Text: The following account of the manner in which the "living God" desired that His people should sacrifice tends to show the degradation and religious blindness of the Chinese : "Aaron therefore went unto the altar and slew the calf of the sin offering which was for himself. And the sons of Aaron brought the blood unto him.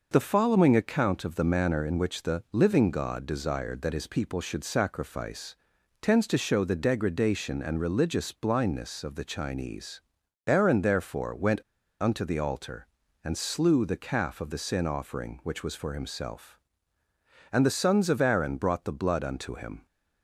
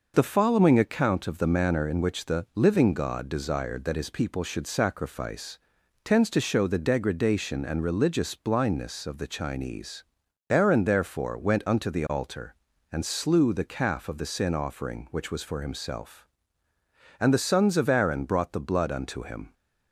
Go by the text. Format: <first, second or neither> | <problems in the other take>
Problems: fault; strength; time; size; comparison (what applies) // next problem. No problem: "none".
second | pauses between "sacrifice" and "tends"; noticeable; at 5.5 s; 0.46 s long; noticeable in the second // pauses between "went" and "unto"; at 11.6 s; 0.41 s long